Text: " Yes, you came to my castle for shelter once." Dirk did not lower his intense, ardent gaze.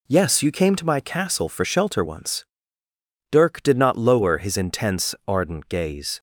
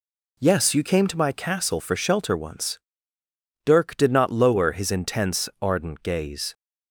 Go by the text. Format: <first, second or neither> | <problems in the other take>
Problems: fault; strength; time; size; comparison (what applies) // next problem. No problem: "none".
neither | none